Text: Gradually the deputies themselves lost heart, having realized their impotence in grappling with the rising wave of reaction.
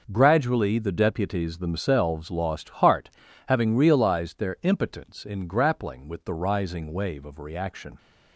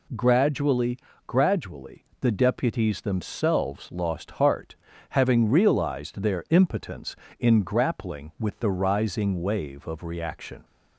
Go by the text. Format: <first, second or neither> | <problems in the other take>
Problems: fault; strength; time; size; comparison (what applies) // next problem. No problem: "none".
first | says "Gradually" twice; at 1.2 s